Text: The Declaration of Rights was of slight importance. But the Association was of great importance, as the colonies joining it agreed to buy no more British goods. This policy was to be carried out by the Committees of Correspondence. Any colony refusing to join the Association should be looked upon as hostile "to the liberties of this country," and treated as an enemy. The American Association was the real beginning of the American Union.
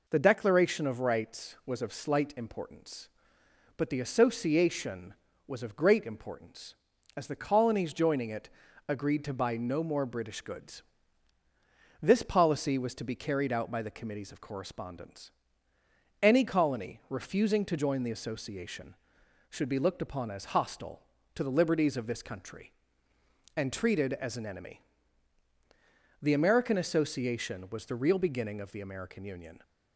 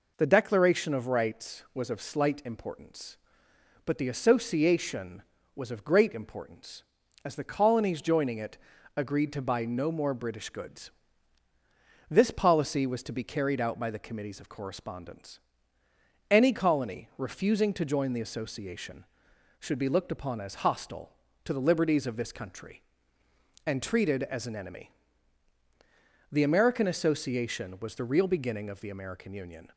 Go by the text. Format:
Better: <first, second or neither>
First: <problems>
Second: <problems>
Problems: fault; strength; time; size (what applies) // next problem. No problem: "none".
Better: neither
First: pauses between "it" and "agreed"; at 8.4 s; 0.40 s long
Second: pauses between "it" and "agreed"; at 8.5 s; 0.40 s long